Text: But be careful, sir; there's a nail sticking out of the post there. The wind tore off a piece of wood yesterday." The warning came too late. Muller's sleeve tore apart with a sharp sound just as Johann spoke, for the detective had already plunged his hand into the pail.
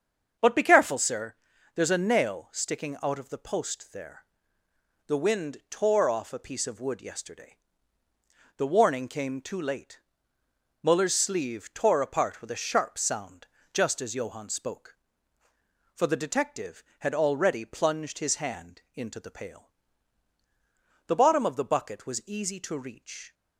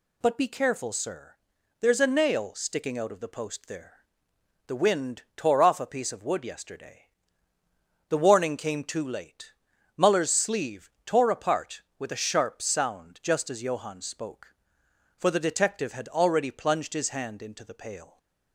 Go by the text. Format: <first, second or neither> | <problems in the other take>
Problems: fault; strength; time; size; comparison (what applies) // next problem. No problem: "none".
second | starts louder than the rest; strong; until 1.8 s; 7 dB // pauses between "sound" and "just"; slight; at 13.4 s; 0.26 s long // goes on to say "The bottom of the bucket was easy to reach"; strong; from 21.0 s on; 2.2 s long